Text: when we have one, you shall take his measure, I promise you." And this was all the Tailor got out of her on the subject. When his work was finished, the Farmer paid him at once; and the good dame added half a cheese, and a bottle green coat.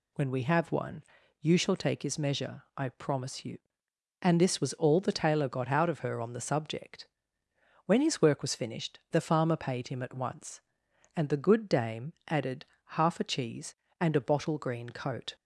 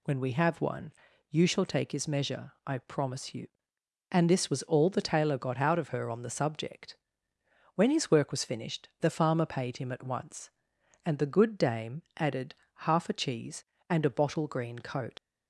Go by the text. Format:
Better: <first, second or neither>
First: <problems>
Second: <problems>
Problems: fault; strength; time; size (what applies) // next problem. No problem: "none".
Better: first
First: pauses between "added" and "half"; slight; at 12.6 s; 0.22 s long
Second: pauses between "added" and "half"; slight; at 12.5 s; 0.22 s long // leaves "coat" unfinished; at 15.1 s; 65 ms